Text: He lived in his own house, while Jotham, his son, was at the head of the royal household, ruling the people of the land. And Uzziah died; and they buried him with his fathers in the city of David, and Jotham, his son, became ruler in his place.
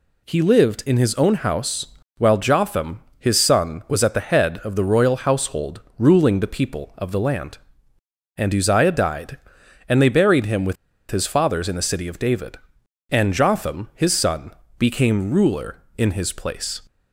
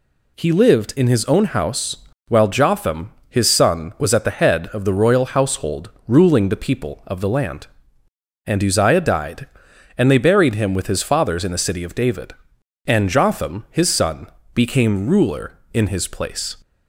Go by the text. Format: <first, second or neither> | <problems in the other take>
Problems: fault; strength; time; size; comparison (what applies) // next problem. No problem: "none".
second | pauses between "with" and "his"; at 10.7 s; 0.36 s long